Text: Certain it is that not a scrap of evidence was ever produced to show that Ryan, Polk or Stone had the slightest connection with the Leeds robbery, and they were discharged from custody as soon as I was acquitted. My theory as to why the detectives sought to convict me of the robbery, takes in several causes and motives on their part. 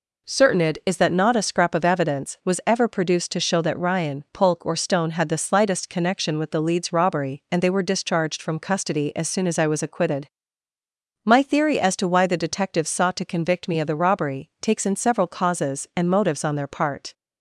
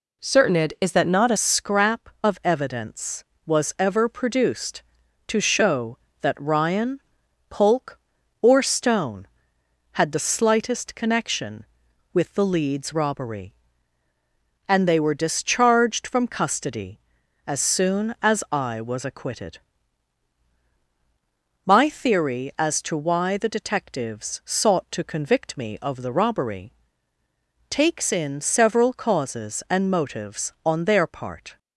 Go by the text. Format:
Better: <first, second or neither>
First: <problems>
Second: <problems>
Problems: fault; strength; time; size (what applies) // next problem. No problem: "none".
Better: first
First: none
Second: changes voice at "scrap"; from 1.3 s on; 30.2 s long